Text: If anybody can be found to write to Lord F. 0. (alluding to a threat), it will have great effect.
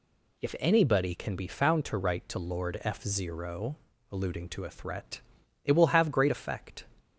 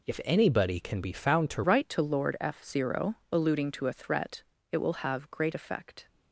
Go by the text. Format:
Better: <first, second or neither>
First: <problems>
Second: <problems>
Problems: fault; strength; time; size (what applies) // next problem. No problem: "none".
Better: first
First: none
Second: changes voice at "write"; from 1.6 s on; 4.4 s long